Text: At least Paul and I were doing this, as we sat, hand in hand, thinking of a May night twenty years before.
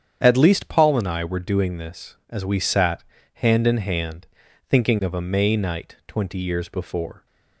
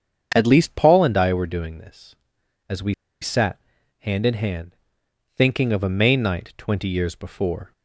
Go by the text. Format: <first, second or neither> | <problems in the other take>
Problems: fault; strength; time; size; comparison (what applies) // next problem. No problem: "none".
first | starts louder than the rest; strong; until 1.3 s; 7.5 dB; strong in the first // pauses between "we" and "sat"; slight; at 2.9 s; 0.27 s long